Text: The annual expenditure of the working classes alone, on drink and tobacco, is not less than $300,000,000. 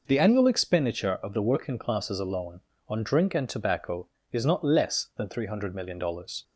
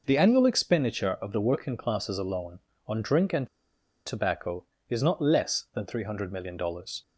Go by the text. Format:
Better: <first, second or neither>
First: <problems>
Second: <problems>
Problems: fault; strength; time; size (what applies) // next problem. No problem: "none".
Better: first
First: none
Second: pauses between "and" and "tobacco"; noticeable; at 3.4 s; 0.58 s long